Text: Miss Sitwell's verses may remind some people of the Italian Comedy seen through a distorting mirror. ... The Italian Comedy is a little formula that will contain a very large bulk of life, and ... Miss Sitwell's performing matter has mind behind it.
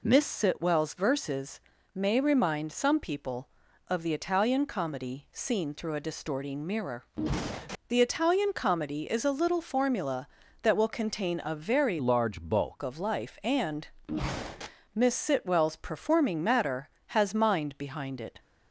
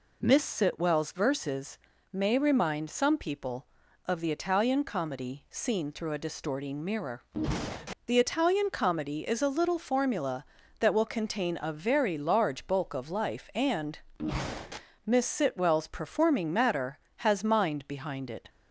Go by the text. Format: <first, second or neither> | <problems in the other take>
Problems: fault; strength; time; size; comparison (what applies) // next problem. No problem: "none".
second | pauses between "verses" and "may"; slight; at 1.6 s; 0.34 s long; slight in the second // changes voice from "large" to "bulk"; from 11.9 to 12.8 s; 0.9 s long